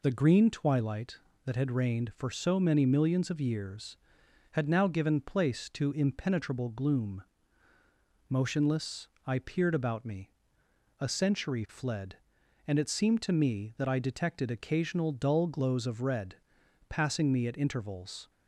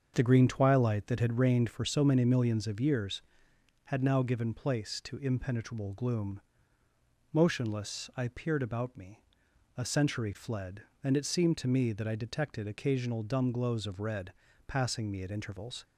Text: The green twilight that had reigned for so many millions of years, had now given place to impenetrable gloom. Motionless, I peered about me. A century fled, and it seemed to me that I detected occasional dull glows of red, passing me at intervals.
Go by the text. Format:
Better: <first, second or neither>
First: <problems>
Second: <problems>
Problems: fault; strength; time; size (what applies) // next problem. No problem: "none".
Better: first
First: none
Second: starts louder than the rest; until 1.1 s; 6.5 dB // says "dumb" for "dull"; at 13.2 s